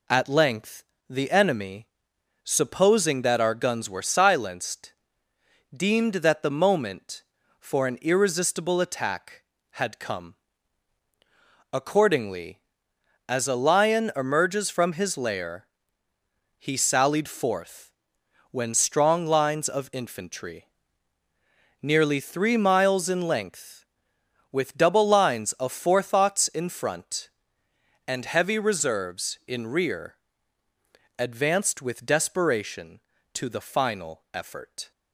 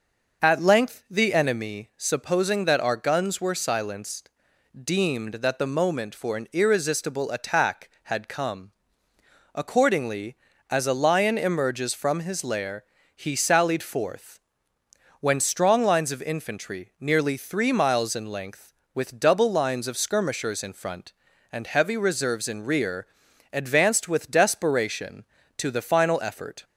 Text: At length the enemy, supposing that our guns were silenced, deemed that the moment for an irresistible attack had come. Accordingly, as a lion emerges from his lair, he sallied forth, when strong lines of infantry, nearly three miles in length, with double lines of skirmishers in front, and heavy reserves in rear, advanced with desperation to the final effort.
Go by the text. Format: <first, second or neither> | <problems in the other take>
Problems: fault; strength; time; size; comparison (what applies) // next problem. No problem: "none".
second | pauses between "length" and "the"; slight; at 0.8 s; 0.26 s long // says "forethoughts" for "skirmishers"; at 25.7 s